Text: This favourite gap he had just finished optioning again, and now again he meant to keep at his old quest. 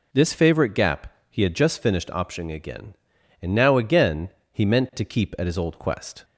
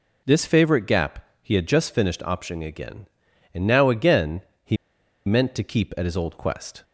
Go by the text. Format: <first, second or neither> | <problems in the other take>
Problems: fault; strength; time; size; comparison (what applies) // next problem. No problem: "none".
first | pauses between "gap" and "he"; slight; at 1.2 s; 0.16 s long; slight in the first // pauses between "again" and "he"; slight; at 4.4 s; 0.22 s long; slight in the first // pauses between "he" and "meant"; noticeable; at 4.7 s; 0.50 s long